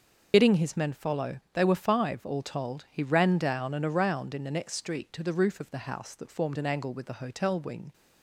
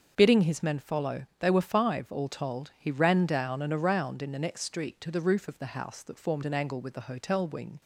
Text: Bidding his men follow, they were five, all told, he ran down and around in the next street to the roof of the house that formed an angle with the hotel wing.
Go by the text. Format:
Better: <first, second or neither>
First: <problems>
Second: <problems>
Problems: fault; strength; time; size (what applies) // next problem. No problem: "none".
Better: second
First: loses the start of "Bidding"; at 0.3 s; 40 ms // starts louder than the rest; noticeable; until 1.3 s; 6 dB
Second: starts louder than the rest; until 1.1 s; 6.5 dB